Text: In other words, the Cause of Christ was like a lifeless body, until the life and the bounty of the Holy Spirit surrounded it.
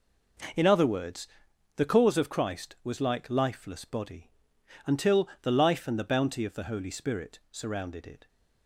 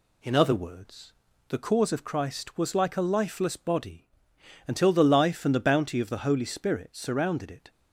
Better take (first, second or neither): second